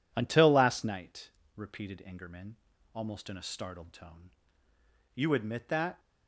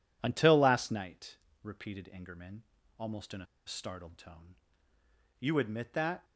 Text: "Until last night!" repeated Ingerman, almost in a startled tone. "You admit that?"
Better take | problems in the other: first | pauses between "a" and "startled"; slight; at 3.4 s; 0.20 s long

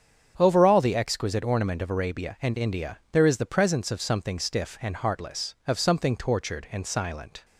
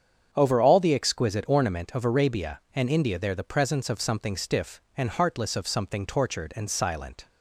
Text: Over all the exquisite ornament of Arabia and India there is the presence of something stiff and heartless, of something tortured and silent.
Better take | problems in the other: first | starts louder than the rest; strong; until 1.3 s; 7.5 dB; strong in the first // skips "is"; at 3.3 s

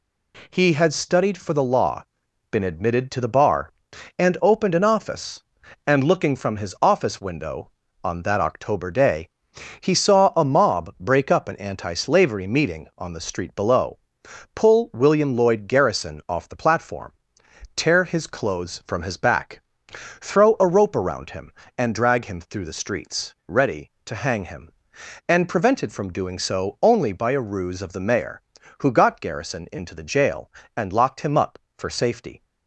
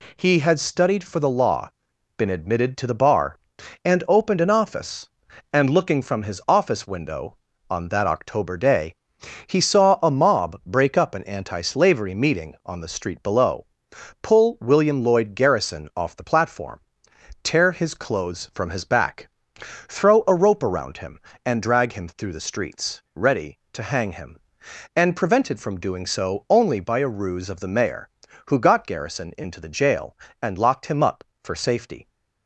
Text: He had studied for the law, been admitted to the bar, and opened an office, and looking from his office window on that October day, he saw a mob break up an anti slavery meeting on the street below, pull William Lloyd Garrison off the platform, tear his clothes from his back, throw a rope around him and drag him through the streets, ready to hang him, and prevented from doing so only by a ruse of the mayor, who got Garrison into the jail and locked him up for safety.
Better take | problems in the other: neither | none

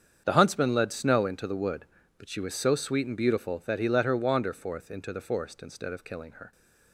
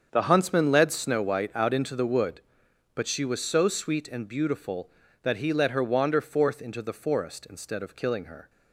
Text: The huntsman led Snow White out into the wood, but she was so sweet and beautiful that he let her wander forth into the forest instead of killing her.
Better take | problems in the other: second | starts louder than the rest; strong; until 1.2 s; 7.5 dB; strong in the second // skips "White out"; at 1.2 s

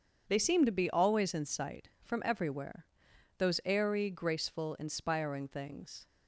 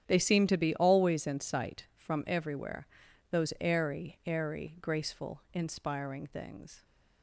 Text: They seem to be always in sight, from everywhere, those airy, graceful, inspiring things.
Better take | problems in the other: first | starts louder than the rest; strong; until 1.0 s; 9.5 dB; strong in the first // says "airy" twice; at 4.2 s

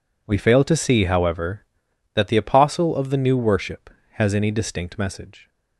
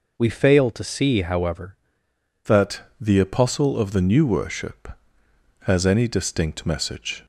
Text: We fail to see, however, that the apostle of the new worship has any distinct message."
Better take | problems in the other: first | changes voice at "that"; from 2.4 s on; 4.8 s long // pauses between "that" and "the"; slight; at 2.8 s; 0.18 s long

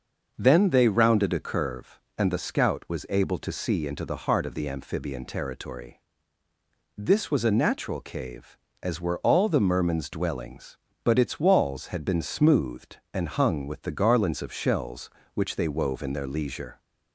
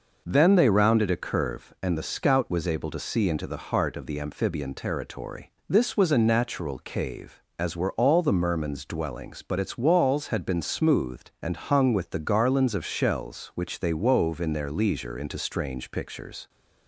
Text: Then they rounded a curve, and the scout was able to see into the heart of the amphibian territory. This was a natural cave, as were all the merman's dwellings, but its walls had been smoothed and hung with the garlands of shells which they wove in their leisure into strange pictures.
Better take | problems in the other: second | stops before "into strange pictures"; at 16.7 s

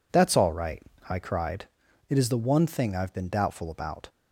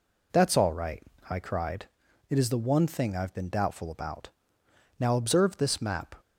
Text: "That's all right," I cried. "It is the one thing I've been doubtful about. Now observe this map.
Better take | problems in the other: second | stops before "Now observe this map"; at 4.0 s

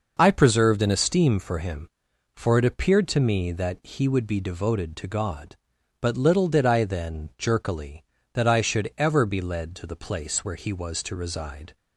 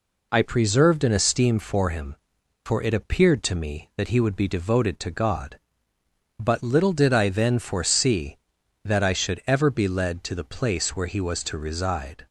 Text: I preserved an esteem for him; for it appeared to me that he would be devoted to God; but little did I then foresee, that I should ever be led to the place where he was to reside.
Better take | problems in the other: second | says "jerkily" for "foresee"; at 7.3 s

